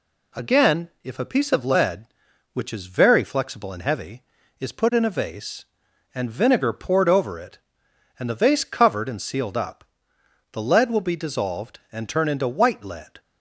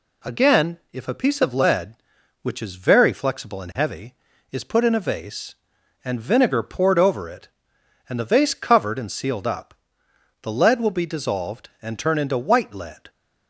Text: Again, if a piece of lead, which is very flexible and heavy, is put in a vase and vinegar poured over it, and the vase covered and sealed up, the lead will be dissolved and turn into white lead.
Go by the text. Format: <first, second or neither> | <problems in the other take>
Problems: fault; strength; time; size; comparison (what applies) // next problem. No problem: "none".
neither | none